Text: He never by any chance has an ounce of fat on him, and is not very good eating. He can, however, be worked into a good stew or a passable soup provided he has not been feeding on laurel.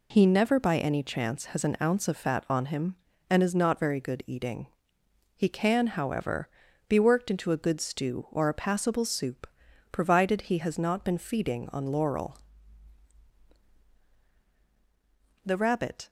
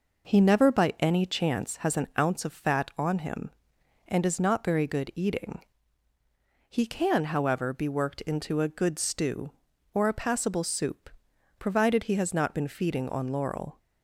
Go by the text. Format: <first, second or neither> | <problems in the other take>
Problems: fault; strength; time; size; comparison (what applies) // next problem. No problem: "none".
second | pauses between "soup" and "provided"; noticeable; at 9.4 s; 0.46 s long; noticeable in the second // goes on to say "The rabbit"; noticeable; from 15.4 s on; 0.64 s long